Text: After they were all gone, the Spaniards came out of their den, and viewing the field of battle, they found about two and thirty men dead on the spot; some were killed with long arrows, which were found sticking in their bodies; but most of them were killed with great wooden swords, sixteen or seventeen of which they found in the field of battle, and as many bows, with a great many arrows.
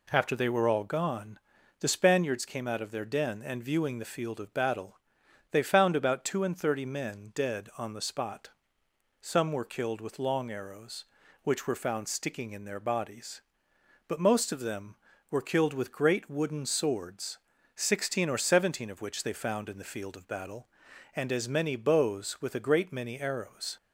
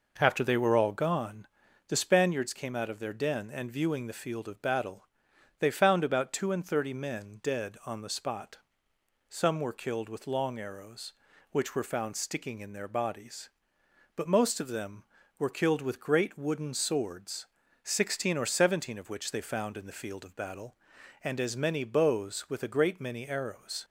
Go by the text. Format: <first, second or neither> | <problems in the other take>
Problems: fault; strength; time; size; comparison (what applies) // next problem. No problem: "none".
first | starts louder than the rest; noticeable; until 1.4 s; 5 dB